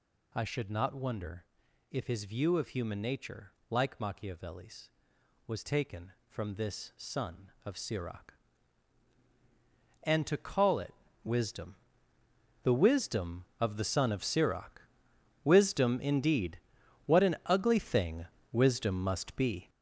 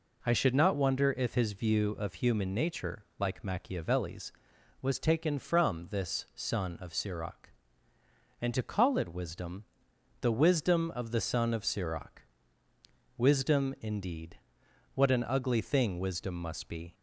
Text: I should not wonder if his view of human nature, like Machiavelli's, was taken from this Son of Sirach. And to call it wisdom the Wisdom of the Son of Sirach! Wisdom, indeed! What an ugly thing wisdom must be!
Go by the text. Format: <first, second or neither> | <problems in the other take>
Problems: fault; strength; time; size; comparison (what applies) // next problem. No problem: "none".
second | gets louder; strong; throughout; 7.5 dB // pauses between "wonder" and "if"; noticeable; at 1.4 s; 0.46 s long // pauses between "it" and "wisdom"; slight; at 10.9 s; 0.30 s long // pauses between "wisdom" and "the"; noticeable; at 11.7 s; 0.88 s long; noticeable in the second // pauses between "thing" and "wisdom"; slight; at 18.2 s; 0.26 s long